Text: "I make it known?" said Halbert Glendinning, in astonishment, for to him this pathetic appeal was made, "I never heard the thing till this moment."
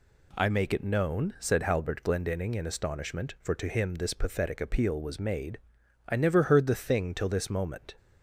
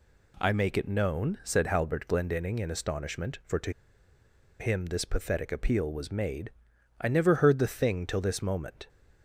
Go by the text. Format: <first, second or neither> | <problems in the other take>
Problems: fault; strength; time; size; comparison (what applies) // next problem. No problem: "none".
first | pauses between "to" and "him"; noticeable; at 3.7 s; 0.88 s long